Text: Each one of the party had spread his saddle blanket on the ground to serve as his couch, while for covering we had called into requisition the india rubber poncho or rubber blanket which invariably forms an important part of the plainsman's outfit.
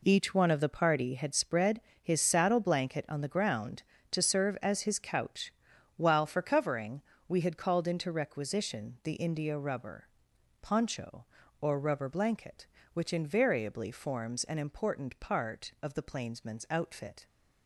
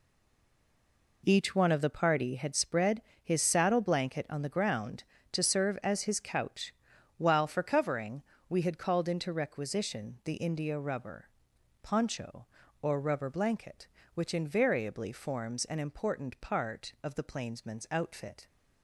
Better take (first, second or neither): first